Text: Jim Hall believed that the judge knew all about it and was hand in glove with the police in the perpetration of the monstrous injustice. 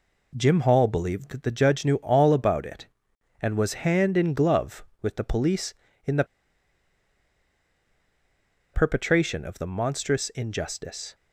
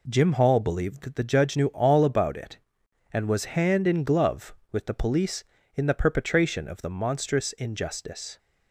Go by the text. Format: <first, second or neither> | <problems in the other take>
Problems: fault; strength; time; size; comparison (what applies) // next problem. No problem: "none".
second | pauses between "the" and "perpetration"; strong; at 6.2 s; 2.4 s long